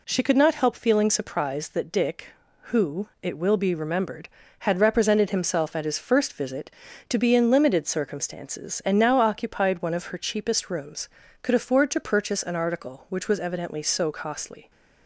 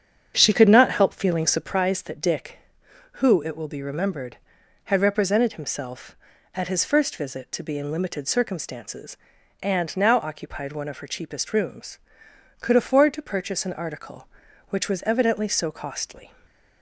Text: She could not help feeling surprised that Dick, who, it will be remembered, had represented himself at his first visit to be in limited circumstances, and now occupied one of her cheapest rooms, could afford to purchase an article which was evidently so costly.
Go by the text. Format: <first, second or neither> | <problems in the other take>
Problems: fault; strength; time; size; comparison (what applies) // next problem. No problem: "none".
first | starts louder than the rest; strong; until 1.7 s; 7.5 dB // stays silent after the last word; slight; from 16.2 s on; 0.6 s long